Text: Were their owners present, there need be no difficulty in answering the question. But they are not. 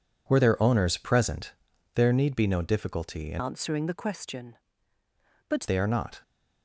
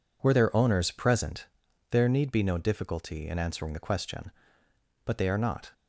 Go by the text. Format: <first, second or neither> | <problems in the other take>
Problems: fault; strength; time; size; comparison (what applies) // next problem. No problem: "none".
second | changes voice from "answering" to "But"; from 3.3 to 5.6 s; 2.3 s long